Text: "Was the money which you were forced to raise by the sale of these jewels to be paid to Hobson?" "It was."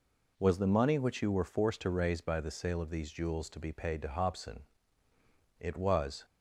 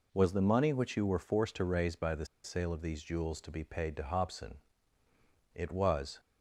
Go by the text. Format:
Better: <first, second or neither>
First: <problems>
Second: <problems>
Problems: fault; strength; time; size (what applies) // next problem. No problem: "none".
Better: first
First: none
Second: pauses between "the" and "sale"; slight; at 2.2 s; 0.18 s long